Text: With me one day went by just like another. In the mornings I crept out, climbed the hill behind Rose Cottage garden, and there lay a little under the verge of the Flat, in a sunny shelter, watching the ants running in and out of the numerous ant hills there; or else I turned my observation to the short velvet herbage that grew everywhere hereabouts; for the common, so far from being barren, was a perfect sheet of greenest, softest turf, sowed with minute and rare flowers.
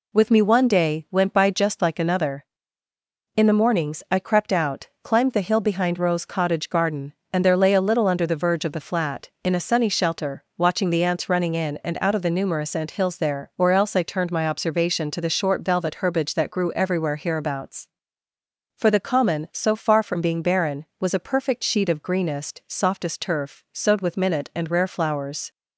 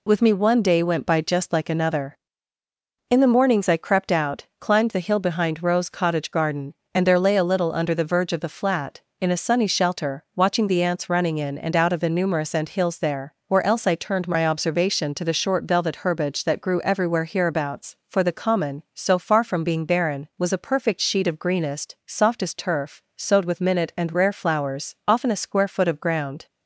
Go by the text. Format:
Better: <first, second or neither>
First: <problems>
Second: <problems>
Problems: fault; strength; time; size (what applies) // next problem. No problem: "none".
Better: first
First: none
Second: goes on to say "Often a square foot of ground"; from 25.0 s on; 1.3 s long